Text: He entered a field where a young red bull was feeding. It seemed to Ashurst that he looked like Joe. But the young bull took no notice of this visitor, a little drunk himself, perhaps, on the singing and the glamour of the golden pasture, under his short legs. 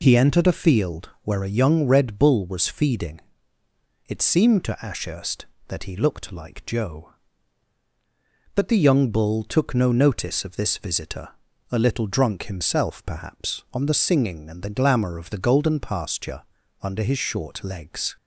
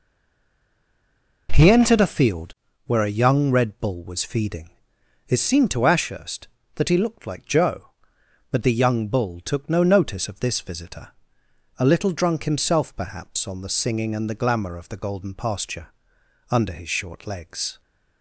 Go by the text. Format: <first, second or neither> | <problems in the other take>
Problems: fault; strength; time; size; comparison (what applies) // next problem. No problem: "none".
first | stays silent before the first word; noticeable; until 1.4 s; 1.4 s long // pauses between "field" and "where"; slight; at 2.5 s; 0.32 s long